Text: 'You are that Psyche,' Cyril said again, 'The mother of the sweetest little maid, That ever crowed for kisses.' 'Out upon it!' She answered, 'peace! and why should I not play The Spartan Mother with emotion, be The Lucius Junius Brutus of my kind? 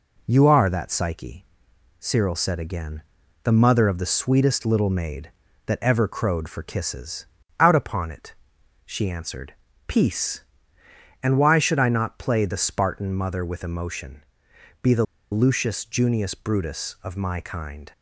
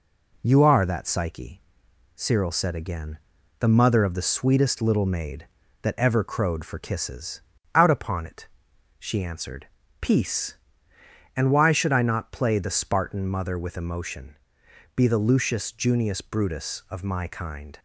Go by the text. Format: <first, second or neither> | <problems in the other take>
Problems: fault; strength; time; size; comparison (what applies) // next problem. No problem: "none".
second | pauses between "The" and "Lucius"; slight; at 15.0 s; 0.28 s long